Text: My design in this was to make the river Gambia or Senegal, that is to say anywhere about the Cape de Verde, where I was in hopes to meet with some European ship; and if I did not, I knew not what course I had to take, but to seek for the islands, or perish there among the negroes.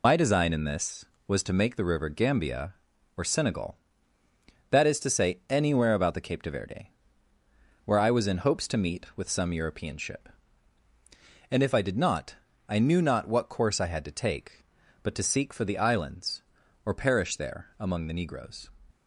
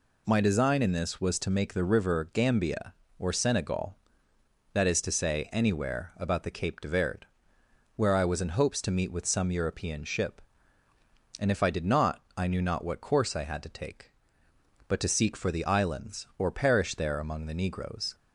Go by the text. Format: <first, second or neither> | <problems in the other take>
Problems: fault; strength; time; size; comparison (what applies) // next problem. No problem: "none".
second | loses the start of "My"; at 0.0 s; 70 ms